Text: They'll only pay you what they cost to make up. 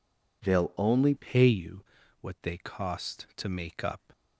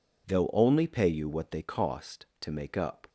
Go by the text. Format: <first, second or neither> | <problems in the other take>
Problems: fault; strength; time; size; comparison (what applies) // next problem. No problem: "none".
second | changes voice at "pay"; from 1.1 s on; 3.0 s long // pauses between "you" and "what"; at 1.8 s; 0.38 s long